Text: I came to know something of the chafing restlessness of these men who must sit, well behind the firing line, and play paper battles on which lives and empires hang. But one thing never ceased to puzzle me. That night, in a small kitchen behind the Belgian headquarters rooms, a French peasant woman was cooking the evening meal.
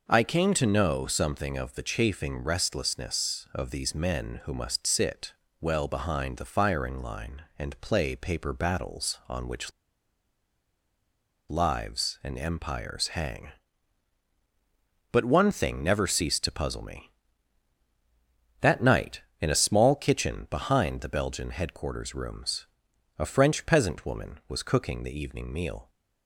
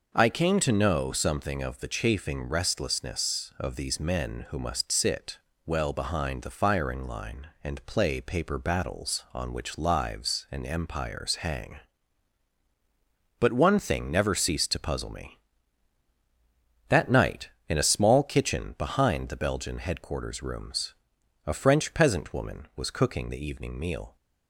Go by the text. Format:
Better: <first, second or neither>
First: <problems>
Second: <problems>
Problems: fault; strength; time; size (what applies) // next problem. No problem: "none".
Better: second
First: pauses between "which" and "lives"; strong; at 9.7 s; 1.7 s long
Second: none